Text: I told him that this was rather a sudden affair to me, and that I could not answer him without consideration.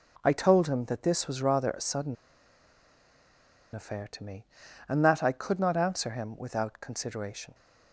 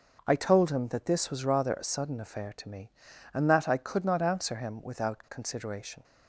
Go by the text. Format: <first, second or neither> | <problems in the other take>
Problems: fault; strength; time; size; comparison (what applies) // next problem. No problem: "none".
second | starts louder than the rest; noticeable; until 1.2 s; 6 dB; noticeable in the second // pauses between "sudden" and "affair"; strong; at 2.1 s; 1.5 s long